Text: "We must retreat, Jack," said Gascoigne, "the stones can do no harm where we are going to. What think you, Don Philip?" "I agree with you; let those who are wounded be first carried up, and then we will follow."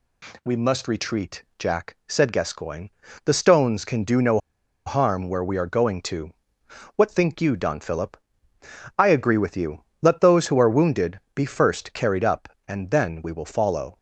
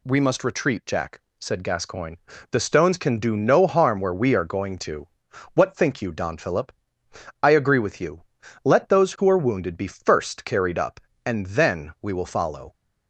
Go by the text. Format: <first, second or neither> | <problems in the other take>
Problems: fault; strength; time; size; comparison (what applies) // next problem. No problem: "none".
second | pauses between "no" and "harm"; noticeable; at 4.3 s; 0.47 s long